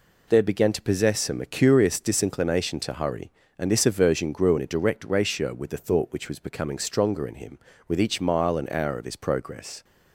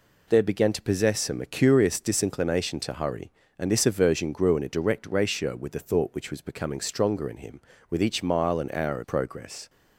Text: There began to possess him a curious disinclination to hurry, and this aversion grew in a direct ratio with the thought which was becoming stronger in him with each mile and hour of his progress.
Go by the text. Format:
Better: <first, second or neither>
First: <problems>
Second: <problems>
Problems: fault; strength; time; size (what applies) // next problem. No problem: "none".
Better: first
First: none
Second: skips "his"; at 9.0 s